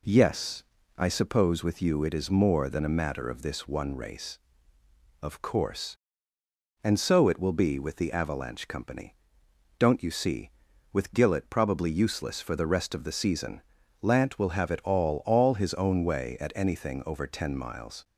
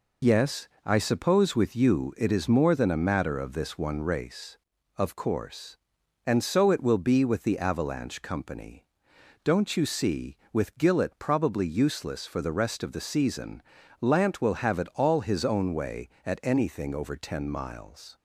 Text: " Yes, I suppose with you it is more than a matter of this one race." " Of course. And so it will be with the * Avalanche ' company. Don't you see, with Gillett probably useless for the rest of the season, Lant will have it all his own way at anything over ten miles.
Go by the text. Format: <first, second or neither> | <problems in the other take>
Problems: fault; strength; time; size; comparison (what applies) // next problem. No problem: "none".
second | says "all" twice; at 15.2 s